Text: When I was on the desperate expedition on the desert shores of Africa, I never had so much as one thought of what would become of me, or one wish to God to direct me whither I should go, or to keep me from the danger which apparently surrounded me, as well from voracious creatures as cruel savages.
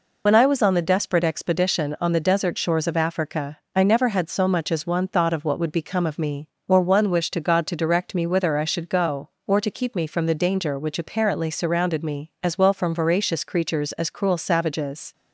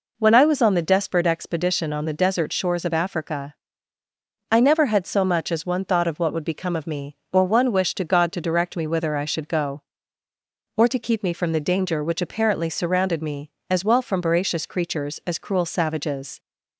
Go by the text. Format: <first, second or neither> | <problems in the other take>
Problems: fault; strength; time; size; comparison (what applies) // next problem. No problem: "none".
second | loses the start of "When"; at 0.2 s; 70 ms